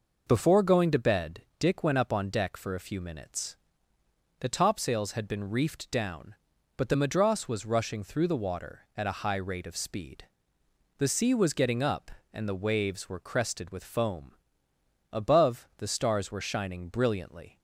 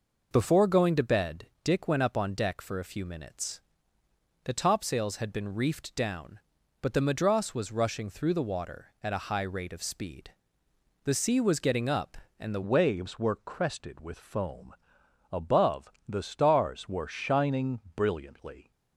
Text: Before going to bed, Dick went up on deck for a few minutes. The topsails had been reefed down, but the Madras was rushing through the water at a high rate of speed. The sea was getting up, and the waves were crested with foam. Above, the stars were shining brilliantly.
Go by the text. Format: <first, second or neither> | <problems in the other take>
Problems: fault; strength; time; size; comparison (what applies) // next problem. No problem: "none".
first | changes voice at "waves"; from 12.6 s on; 6.1 s long // pauses between "shining" and "brilliantly"; slight; at 17.7 s; 0.16 s long